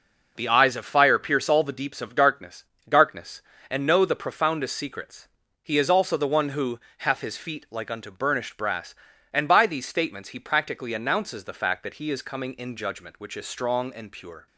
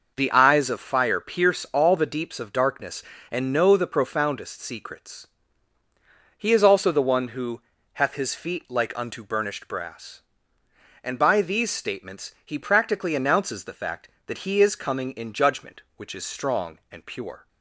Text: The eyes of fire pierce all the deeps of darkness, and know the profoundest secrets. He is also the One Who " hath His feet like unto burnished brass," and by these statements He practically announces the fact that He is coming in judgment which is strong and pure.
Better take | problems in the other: second | says "darkness" twice; at 2.8 s

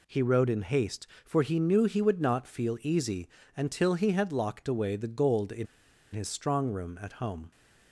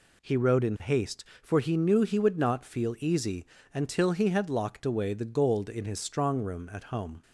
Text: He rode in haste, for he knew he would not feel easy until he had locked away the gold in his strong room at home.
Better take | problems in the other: second | pauses between "easy" and "until"; slight; at 3.2 s; 0.30 s long; slight in the second // pauses between "in" and "his"; noticeable; at 5.6 s; 0.46 s long

